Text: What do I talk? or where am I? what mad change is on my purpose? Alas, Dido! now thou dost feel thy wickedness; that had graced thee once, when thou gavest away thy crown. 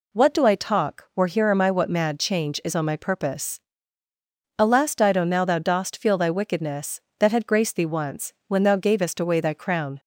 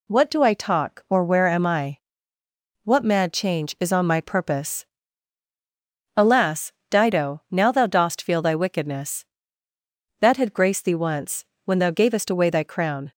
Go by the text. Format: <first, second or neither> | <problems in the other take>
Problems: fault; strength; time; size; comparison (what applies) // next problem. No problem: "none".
second | says "here" for "where"; at 1.2 s